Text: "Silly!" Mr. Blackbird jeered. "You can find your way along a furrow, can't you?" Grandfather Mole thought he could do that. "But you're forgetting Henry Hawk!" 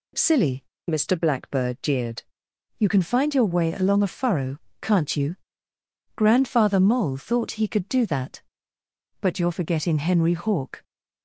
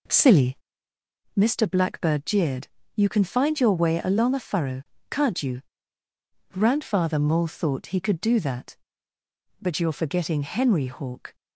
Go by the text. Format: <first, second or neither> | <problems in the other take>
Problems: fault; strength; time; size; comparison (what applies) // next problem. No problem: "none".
first | starts louder than the rest; noticeable; until 1.2 s; 4 dB